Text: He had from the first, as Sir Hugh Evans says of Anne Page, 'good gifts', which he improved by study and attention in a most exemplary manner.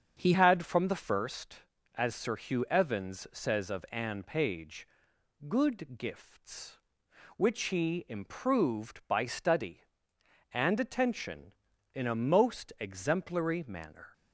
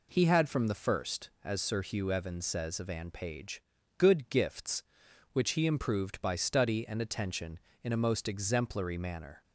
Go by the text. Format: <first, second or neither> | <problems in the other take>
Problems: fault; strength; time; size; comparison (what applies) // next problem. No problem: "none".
second | starts louder than the rest; until 1.2 s; 7 dB // changes voice at "had"; from 0.3 s on; 13.8 s long